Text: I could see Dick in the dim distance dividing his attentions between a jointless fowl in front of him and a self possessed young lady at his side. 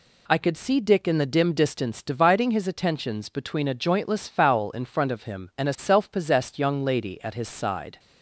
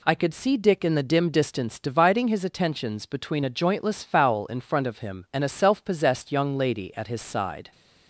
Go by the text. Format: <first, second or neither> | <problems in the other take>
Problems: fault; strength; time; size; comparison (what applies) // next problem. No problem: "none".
neither | none